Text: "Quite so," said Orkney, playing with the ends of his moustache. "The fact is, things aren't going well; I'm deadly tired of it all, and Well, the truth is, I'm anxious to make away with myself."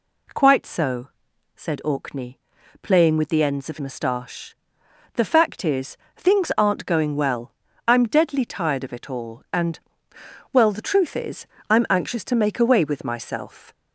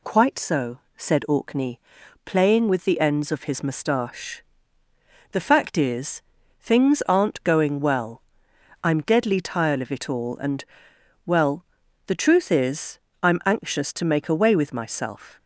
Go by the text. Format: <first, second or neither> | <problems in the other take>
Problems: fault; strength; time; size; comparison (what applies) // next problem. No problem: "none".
second | skips "his"; at 3.7 s // pauses between "and" and "Well"; noticeable; at 9.8 s; 0.72 s long; noticeable in the second